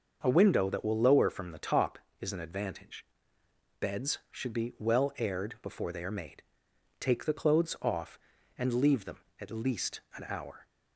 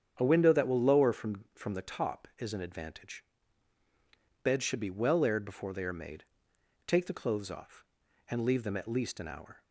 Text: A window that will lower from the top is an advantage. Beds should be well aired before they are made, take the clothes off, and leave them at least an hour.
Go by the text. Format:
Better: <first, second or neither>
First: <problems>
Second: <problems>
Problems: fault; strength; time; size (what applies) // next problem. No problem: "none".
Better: first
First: starts louder than the rest; until 1.2 s; 6 dB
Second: starts louder than the rest; strong; until 1.1 s; 8 dB // says "from" twice; at 1.5 s